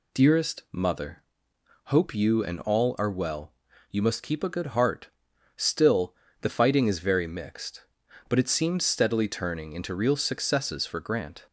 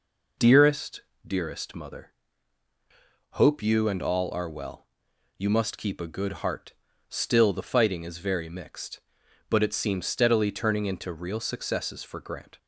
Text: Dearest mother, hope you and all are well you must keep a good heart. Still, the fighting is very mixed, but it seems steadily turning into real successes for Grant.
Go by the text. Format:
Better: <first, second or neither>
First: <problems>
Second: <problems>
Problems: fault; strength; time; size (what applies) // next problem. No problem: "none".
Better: first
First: pauses between "well" and "you"; at 3.5 s; 0.40 s long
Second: says "Dearest" twice; at 1.2 s // pauses between "well" and "you"; noticeable; at 4.8 s; 0.52 s long